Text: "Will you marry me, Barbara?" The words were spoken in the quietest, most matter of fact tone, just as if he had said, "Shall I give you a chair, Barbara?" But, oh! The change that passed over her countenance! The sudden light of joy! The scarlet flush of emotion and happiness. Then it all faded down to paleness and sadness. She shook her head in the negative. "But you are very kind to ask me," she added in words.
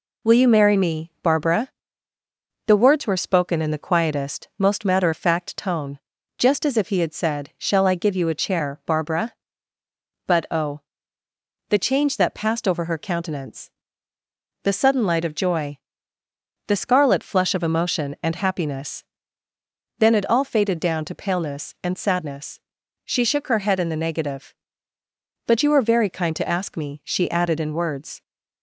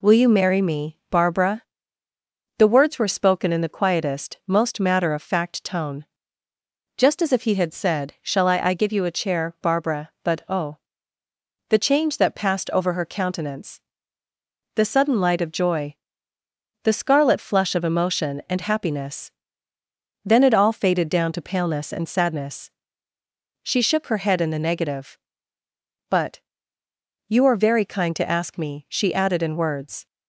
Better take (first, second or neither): first